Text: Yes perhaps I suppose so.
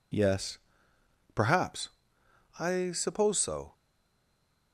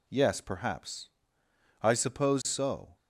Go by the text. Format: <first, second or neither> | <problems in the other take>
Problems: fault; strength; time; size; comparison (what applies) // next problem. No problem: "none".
second | pauses between "Yes" and "perhaps"; noticeable; at 0.5 s; 0.74 s long // pauses between "perhaps" and "I"; noticeable; at 1.8 s; 0.72 s long; noticeable in the second // stays silent after the last word; from 3.7 s on; 1.0 s long